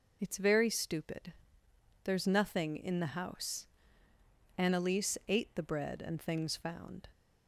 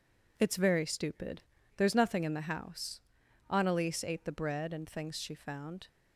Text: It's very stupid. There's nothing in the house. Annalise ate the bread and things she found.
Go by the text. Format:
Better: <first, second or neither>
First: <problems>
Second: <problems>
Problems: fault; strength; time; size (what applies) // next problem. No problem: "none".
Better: second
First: skips "she"; at 6.5 s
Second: none